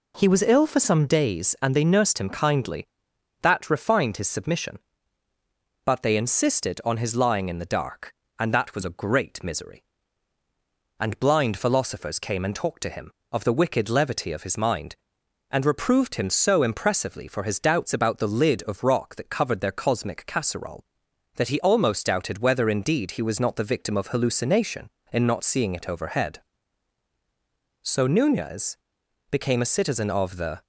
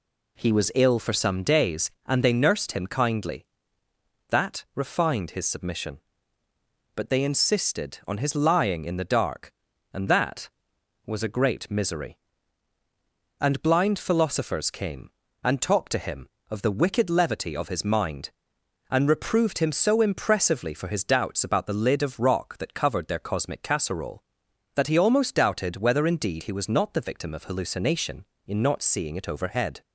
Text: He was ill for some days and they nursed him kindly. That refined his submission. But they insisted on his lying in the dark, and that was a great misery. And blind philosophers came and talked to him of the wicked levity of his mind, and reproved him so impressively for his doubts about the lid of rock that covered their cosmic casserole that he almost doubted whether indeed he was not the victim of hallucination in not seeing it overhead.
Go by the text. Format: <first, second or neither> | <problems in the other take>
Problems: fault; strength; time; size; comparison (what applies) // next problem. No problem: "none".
second | goes on to say "So Nunez became a citizen of the"; strong; from 27.8 s on; 2.8 s long